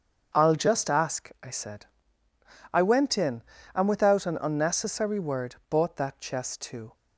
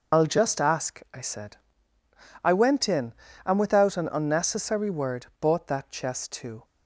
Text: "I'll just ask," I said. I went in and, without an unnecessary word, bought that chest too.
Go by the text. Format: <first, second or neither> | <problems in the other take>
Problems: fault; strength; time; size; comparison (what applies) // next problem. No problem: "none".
first | loses the start of "I'll"; at 0.1 s; 70 ms // starts louder than the rest; noticeable; until 1.2 s; 6 dB; strong in the first